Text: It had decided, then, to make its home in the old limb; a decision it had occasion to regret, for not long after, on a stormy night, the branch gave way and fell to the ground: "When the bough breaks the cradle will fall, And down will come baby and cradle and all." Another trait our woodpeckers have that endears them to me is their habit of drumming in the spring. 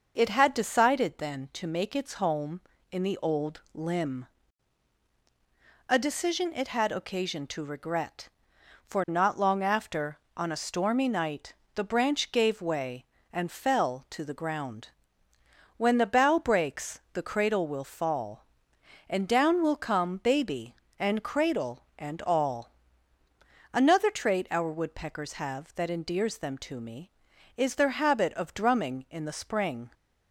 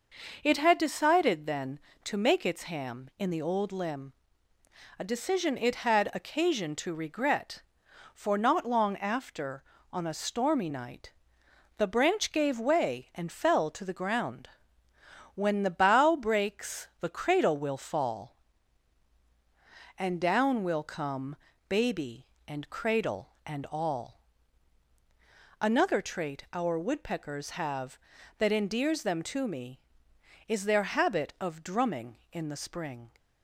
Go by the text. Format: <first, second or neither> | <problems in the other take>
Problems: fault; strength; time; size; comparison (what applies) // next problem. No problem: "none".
first | says "ham" for "home"; at 2.6 s // pauses between "come" and "baby"; slight; at 21.3 s; 0.32 s long